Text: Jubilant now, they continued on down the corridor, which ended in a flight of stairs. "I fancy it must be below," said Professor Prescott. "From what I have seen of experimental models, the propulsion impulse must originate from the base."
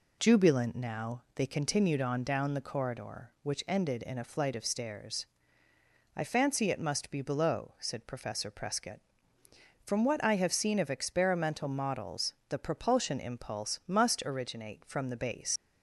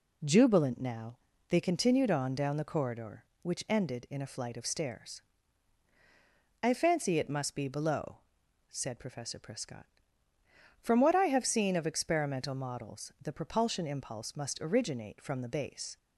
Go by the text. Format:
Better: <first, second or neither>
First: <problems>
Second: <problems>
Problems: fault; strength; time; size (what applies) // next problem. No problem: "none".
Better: second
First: leaves "base" unfinished; at 15.5 s; 80 ms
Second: none